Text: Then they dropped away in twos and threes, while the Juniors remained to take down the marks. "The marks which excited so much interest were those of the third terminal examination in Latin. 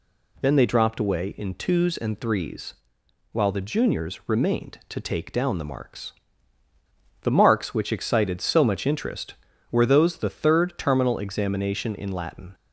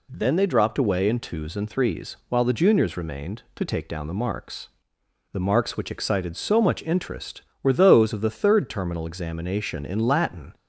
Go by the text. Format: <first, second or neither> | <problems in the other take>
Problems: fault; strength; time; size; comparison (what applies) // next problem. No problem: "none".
second | skips "of"; at 10.1 s